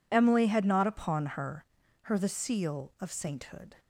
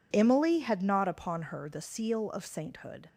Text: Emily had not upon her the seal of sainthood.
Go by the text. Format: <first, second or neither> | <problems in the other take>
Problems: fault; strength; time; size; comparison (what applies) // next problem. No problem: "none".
second | says "her" twice; at 2.0 s